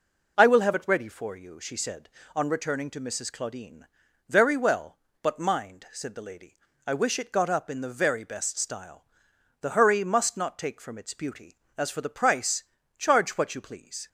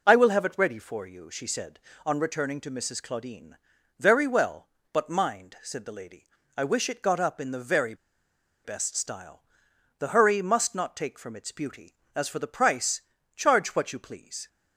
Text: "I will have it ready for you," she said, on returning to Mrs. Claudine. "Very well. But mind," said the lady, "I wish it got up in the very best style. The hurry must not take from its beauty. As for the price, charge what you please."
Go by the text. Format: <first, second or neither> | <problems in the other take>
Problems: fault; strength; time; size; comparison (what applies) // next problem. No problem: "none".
first | pauses between "very" and "best"; noticeable; at 7.9 s; 0.70 s long